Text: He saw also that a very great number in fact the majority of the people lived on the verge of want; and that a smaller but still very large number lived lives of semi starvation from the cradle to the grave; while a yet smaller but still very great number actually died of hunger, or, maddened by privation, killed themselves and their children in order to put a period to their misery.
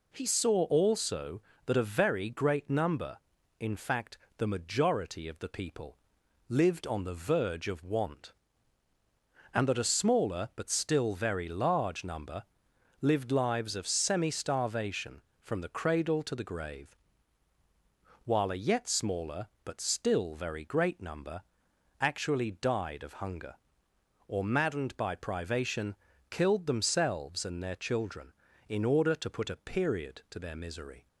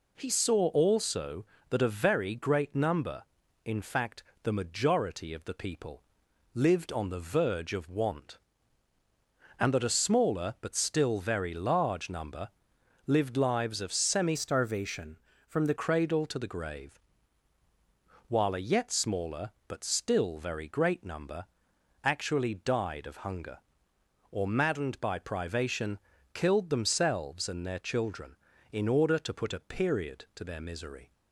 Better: first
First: pauses between "fact" and "the"; slight; at 4.1 s; 0.22 s long // pauses between "people" and "lived"; noticeable; at 5.9 s; 0.52 s long // pauses between "number" and "lived"; noticeable; at 12.4 s; 0.58 s long // pauses between "number" and "actually"; noticeable; at 21.4 s; 0.58 s long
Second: pauses between "fact" and "the"; slight; at 4.2 s; 0.22 s long // pauses between "people" and "lived"; noticeable; at 6.0 s; 0.52 s long // pauses between "number" and "lived"; noticeable; at 12.4 s; 0.58 s long // changes voice from "starvation" to "the"; from 14.3 to 15.7 s; 1.4 s long // pauses between "number" and "actually"; noticeable; at 21.4 s; 0.58 s long

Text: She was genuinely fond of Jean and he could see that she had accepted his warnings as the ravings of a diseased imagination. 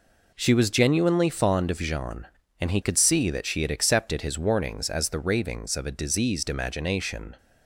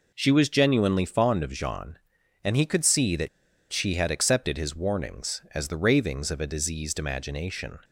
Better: first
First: none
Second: pauses between "that" and "she"; at 3.2 s; 0.43 s long

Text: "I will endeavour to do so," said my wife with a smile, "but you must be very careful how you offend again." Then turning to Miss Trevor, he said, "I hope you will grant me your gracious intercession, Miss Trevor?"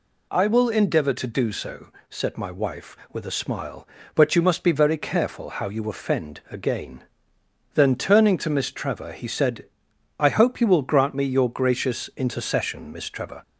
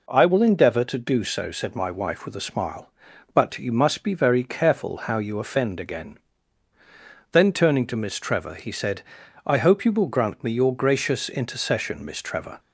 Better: neither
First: none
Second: none

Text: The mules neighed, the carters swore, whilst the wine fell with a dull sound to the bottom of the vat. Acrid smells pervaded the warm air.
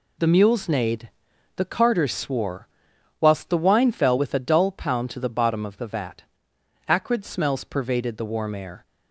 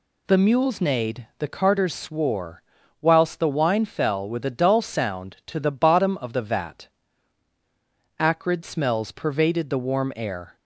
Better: second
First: says "pound" for "sound"; at 4.7 s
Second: none

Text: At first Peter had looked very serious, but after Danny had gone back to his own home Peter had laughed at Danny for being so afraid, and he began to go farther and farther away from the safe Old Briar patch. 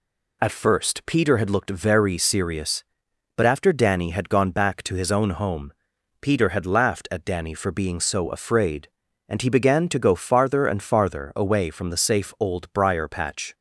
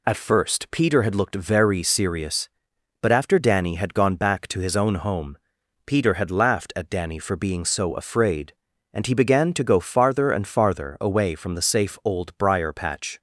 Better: neither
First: pauses between "home" and "Peter"; noticeable; at 5.7 s; 0.48 s long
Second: pauses between "home" and "Peter"; noticeable; at 5.3 s; 0.48 s long

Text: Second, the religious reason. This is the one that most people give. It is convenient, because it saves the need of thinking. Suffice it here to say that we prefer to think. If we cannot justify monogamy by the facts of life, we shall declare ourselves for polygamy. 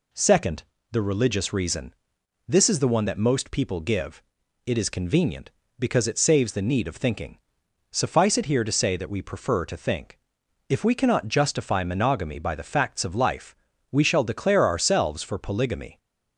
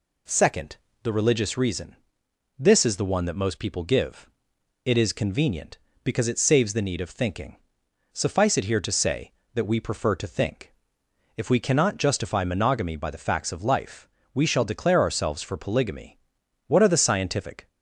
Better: first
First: none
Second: goes on to say "What are the scientific"; noticeable; from 16.6 s on; 1.0 s long

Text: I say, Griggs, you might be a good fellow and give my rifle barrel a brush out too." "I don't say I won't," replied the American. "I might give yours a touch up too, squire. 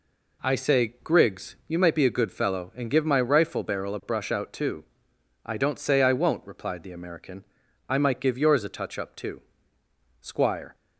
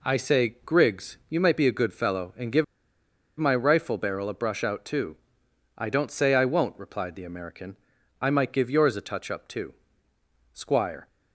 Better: first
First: none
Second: pauses between "give" and "my"; noticeable; at 2.6 s; 0.74 s long

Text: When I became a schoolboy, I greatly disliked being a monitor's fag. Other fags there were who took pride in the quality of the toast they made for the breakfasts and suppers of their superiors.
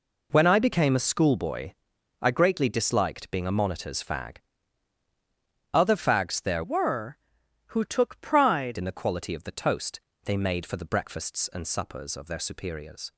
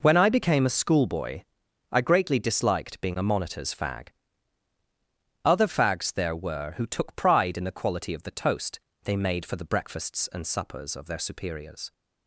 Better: second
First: changes voice from "were" to "pride"; from 6.6 to 8.7 s; 2.1 s long // pauses between "toast" and "they"; slight; at 10.0 s; 0.24 s long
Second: pauses between "toast" and "they"; slight; at 8.8 s; 0.24 s long

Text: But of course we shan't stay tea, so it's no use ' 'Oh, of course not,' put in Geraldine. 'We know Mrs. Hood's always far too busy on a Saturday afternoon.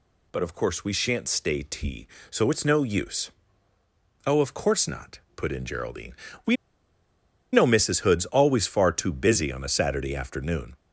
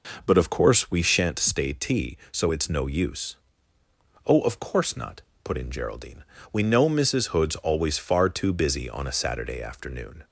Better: second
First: pauses between "We" and "know"; noticeable; at 6.5 s; 0.97 s long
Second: none

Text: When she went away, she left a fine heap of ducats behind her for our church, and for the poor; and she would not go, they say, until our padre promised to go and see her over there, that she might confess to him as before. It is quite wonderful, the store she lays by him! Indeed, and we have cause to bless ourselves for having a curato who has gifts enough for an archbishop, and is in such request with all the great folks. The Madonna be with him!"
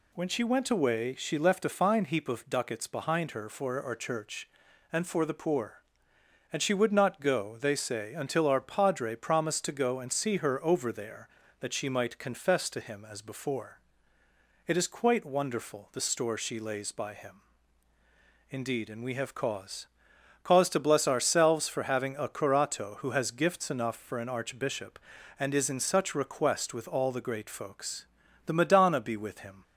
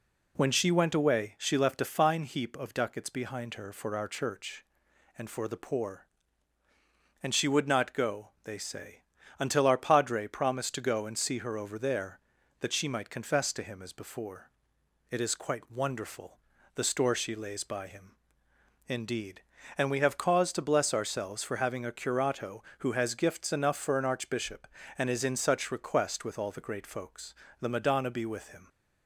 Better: second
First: says "cause" twice; at 20.4 s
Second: none

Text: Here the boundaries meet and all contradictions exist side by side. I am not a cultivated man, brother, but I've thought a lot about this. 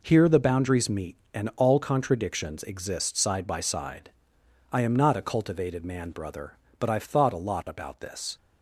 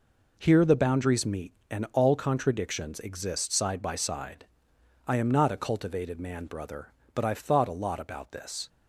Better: neither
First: none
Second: none

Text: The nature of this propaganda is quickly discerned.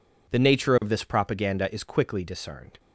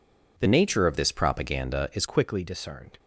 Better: first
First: none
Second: changes voice from "nature" to "is"; from 0.4 to 2.0 s; 1.6 s long

